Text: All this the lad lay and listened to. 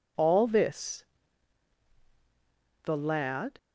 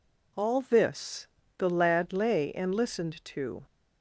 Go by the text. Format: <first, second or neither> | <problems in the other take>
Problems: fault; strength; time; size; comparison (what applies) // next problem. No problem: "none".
second | pauses between "this" and "the"; strong; at 1.0 s; 1.7 s long; slight in the second // stops before "lay and listened to"; at 3.5 s